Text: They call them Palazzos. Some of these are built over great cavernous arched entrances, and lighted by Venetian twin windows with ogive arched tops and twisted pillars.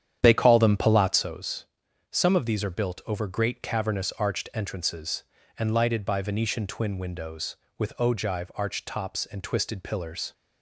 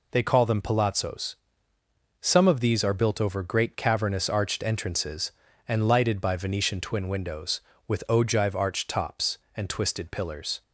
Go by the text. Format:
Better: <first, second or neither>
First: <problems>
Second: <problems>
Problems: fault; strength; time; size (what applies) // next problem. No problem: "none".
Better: second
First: starts louder than the rest; strong; until 1.3 s; 9.5 dB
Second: none